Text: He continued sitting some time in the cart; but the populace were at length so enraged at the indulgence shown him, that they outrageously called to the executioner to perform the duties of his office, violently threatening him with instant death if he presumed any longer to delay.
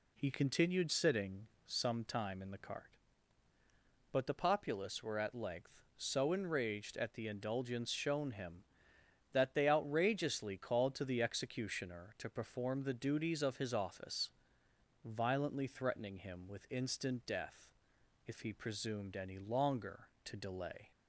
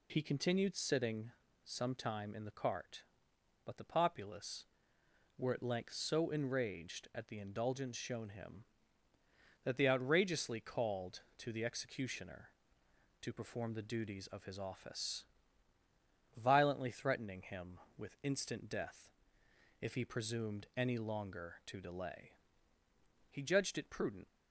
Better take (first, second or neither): first